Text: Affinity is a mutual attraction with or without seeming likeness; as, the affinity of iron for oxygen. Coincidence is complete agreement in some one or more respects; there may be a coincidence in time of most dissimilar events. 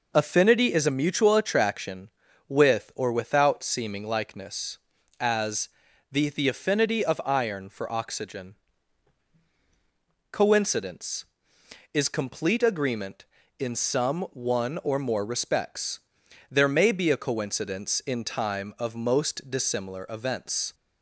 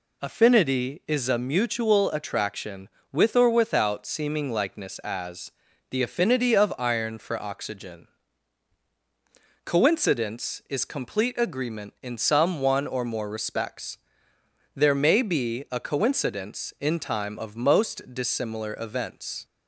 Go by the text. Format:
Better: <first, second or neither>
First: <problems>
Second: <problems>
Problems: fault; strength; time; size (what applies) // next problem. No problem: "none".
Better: second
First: says "the" twice; at 6.2 s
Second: none